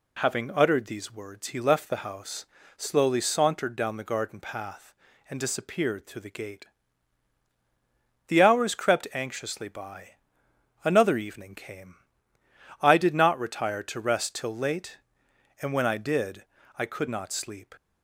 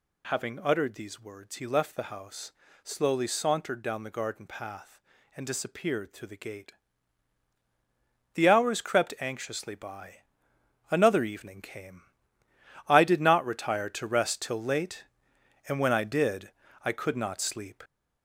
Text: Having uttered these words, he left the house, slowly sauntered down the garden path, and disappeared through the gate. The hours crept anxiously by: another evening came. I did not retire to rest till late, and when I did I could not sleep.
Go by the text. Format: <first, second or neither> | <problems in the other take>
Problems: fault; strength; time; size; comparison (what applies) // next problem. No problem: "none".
first | gets louder; noticeable; throughout; 5.5 dB // pauses between "did" and "I"; slight; at 16.5 s; 0.34 s long; slight in the first